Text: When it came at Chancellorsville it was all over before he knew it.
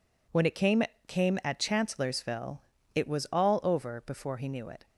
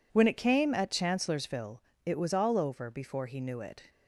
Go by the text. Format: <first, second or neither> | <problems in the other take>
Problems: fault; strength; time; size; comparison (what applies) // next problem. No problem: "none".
second | says "came" twice; at 1.0 s // pauses between "Chancellorsville" and "it"; slight; at 2.6 s; 0.34 s long; slight in the second